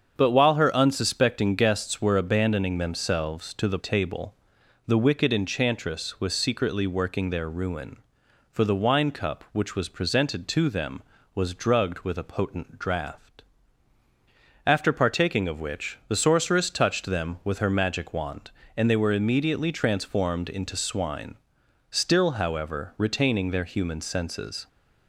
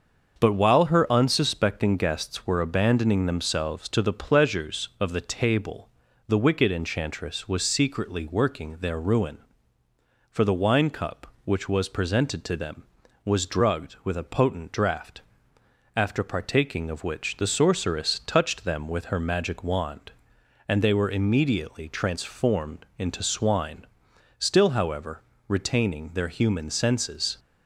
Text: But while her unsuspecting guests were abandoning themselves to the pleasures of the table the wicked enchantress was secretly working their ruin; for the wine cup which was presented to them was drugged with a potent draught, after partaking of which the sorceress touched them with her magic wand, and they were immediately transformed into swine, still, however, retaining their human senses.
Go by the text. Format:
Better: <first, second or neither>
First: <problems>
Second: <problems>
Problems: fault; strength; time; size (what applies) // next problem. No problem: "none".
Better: second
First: starts louder than the rest; strong; until 1.1 s; 7 dB // skips "pleasures of the"; at 3.7 s // pauses between "table" and "the"; noticeable; at 4.3 s; 0.50 s long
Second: starts louder than the rest; until 1.4 s; 6.5 dB // pauses between "table" and "the"; at 5.8 s; 0.40 s long